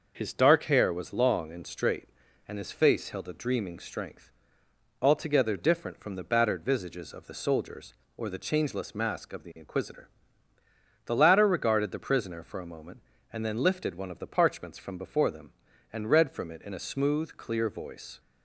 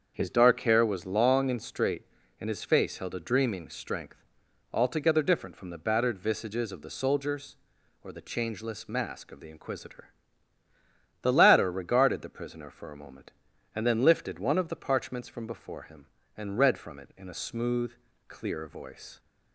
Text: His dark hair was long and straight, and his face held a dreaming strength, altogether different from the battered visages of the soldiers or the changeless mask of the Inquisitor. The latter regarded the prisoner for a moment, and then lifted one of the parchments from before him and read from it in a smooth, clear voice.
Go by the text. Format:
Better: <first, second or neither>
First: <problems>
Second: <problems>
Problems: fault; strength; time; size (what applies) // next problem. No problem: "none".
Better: second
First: starts louder than the rest; noticeable; until 1.1 s; 6 dB // says "them" for "him"; at 15.2 s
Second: starts louder than the rest; until 1.1 s; 7 dB